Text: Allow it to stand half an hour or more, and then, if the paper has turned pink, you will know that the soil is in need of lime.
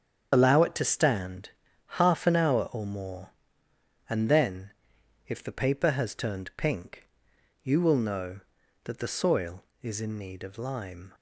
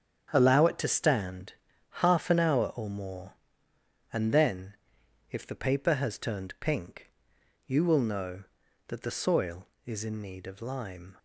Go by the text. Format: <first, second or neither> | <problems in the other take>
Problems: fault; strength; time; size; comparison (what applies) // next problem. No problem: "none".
second | loses the start of "Allow"; at 0.3 s; 80 ms // starts louder than the rest; strong; until 1.3 s; 7.5 dB; strong in the second // pauses between "stand" and "half"; slight; at 1.4 s; 0.36 s long; slight in the second